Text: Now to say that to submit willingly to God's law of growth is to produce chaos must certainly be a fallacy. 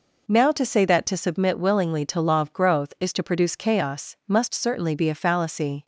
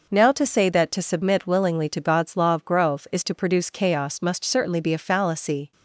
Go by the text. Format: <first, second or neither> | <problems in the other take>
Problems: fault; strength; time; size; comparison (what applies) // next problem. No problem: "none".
second | skips "God's"; at 2.2 s